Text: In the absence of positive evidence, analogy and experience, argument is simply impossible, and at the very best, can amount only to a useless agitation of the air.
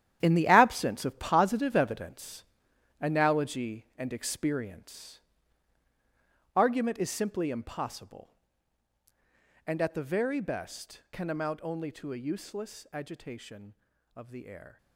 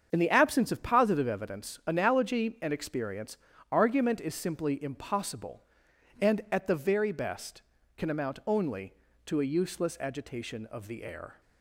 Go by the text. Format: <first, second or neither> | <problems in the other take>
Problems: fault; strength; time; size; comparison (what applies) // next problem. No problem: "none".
second | gets quieter; strong; throughout; 11.5 dB // starts louder than the rest; strong; until 1.2 s; 10.5 dB; strong in the second